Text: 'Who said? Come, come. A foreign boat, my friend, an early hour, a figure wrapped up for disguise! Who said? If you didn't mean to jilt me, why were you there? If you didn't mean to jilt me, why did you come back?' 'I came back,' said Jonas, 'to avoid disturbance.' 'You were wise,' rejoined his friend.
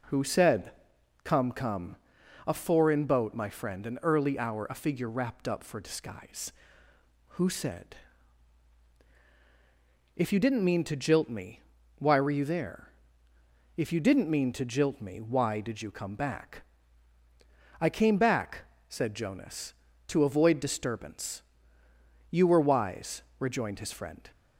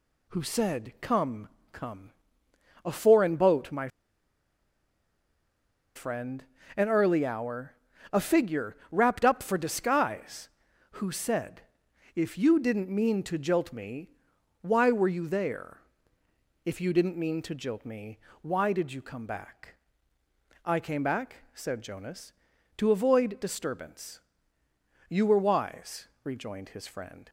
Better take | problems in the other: first | pauses between "my" and "friend"; strong; at 3.8 s; 2.0 s long // pauses between "figure" and "wrapped"; slight; at 8.7 s; 0.16 s long

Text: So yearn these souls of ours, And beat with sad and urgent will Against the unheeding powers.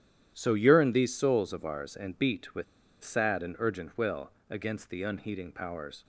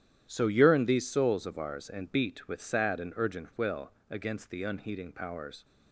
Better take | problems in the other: second | starts louder than the rest; strong; until 1.3 s; 11 dB; strong in the second // pauses between "with" and "sad"; at 2.6 s; 0.39 s long // pauses between "will" and "Against"; slight; at 4.2 s; 0.18 s long; slight in the second

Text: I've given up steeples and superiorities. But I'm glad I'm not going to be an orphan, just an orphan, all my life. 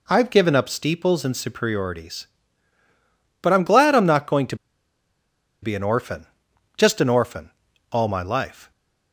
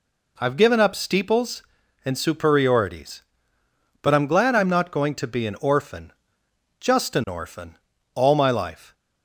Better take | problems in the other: second | pauses between "to" and "be"; at 4.5 s; 1.0 s long

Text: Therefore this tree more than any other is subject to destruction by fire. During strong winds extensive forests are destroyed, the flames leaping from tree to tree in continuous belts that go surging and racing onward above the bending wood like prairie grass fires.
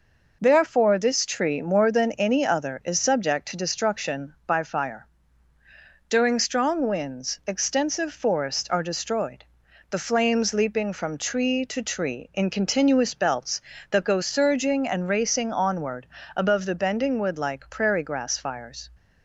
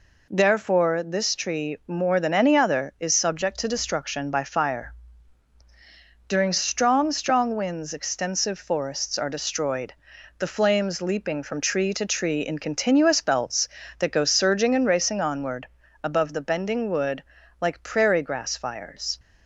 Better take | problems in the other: first | says "strong" twice; at 7.1 s // pauses between "onward" and "above"; at 15.6 s; 0.38 s long; slight in the first // pauses between "wood" and "like"; at 17.2 s; 0.38 s long

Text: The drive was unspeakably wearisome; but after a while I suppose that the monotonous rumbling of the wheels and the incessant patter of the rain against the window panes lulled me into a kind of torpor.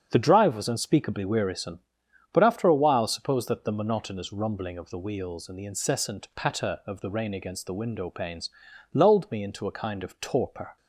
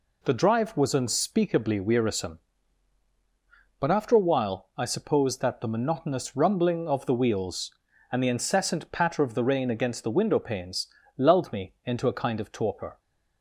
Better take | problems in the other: second | starts louder than the rest; until 1.1 s; 7 dB // skips "I"; at 3.0 s // pauses between "panes" and "lulled"; noticeable; at 8.4 s; 0.46 s long; slight in the second

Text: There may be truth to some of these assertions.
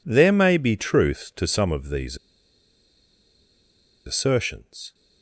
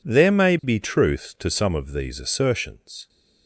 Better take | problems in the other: second | pauses between "these" and "assertions"; strong; at 2.1 s; 1.8 s long

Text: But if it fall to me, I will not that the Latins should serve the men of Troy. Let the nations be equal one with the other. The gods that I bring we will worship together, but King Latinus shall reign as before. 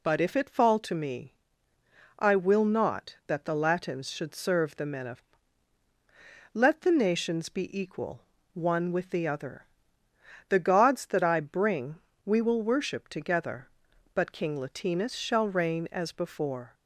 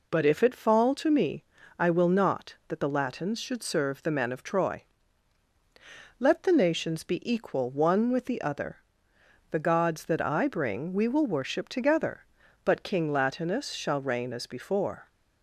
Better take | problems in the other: second | skips "Troy"; at 5.8 s // pauses between "equal" and "one"; slight; at 8.2 s; 0.32 s long // pauses between "bring" and "we"; slight; at 11.9 s; 0.30 s long

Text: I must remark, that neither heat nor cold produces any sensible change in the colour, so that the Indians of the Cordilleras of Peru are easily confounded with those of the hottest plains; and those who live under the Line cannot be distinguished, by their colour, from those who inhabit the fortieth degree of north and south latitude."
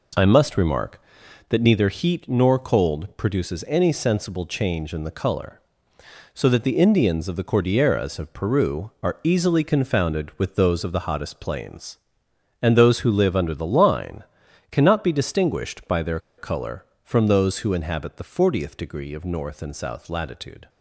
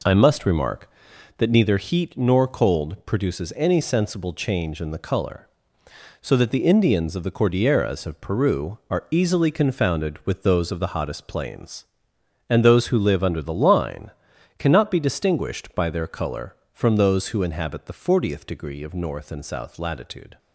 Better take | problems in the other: second | pauses between "Line" and "cannot"; noticeable; at 14.2 s; 0.46 s long; noticeable in the second // pauses between "their" and "colour"; slight; at 16.1 s; 0.18 s long

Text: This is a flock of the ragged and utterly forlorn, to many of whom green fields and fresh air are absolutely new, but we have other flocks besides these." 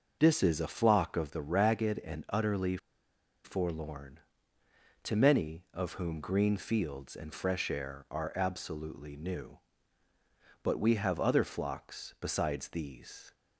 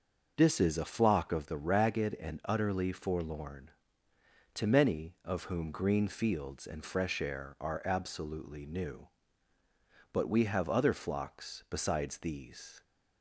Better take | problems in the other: second | starts louder than the rest; noticeable; until 1.2 s; 6 dB; noticeable in the second // pauses between "utterly" and "forlorn"; noticeable; at 2.7 s; 0.67 s long

